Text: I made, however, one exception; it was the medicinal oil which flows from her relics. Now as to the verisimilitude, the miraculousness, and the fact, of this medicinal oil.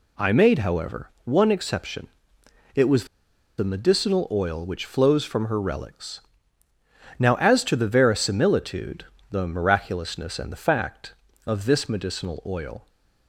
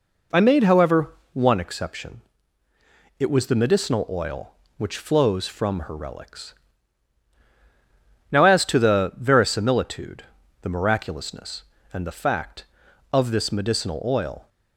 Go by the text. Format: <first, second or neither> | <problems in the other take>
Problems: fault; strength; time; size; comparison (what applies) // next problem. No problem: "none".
second | pauses between "was" and "the"; noticeable; at 3.0 s; 0.53 s long